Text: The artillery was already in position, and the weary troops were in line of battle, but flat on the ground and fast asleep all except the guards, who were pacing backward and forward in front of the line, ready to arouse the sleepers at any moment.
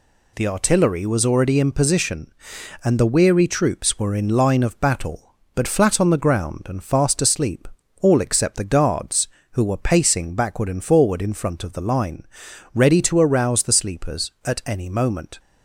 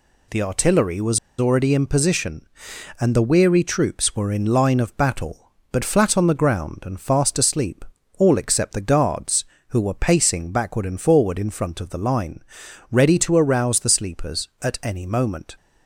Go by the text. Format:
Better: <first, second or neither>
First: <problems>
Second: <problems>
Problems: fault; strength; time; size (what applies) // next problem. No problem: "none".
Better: first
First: pauses between "asleep" and "all"; slight; at 7.6 s; 0.36 s long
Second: pauses between "was" and "already"; slight; at 1.1 s; 0.21 s long // pauses between "asleep" and "all"; slight; at 7.8 s; 0.36 s long